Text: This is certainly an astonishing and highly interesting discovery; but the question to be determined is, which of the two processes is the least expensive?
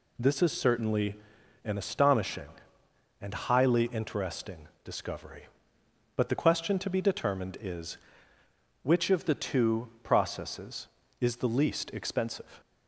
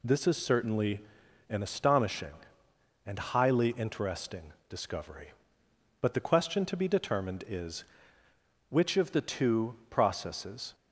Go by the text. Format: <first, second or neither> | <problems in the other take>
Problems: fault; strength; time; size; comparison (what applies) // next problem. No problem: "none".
first | pauses between "certainly" and "an"; noticeable; at 1.0 s; 0.48 s long; noticeable in the first // pauses between "interesting" and "discovery"; slight; at 4.5 s; 0.16 s long; slight in the first // stops before "is the least expensive"; at 10.7 s